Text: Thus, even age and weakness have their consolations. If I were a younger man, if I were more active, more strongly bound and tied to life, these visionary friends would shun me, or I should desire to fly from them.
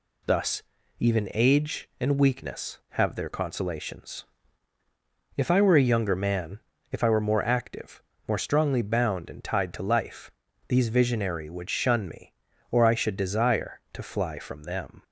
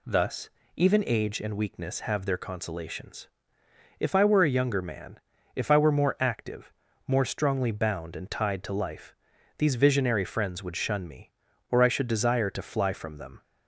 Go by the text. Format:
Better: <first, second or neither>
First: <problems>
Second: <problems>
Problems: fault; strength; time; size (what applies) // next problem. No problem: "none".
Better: second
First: skips "friends"; at 11.4 s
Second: none